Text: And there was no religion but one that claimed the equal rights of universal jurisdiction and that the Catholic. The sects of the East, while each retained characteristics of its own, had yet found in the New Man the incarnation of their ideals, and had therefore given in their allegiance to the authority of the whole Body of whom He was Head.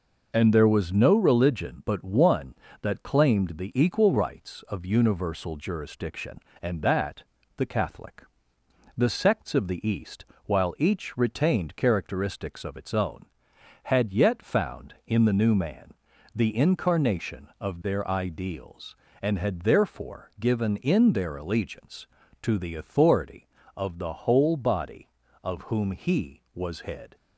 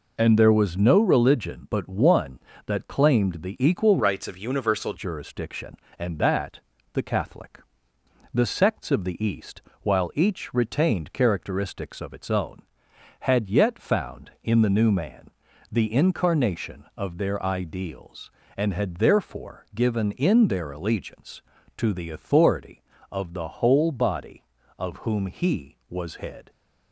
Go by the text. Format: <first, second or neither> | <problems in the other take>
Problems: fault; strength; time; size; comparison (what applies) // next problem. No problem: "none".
first | changes voice from "rights" to "universal"; from 3.9 to 4.9 s; 1.0 s long // pauses between "that" and "the"; slight; at 6.6 s; 0.34 s long; slight in the first // pauses between "Man" and "the"; at 15.2 s; 0.42 s long; also in the first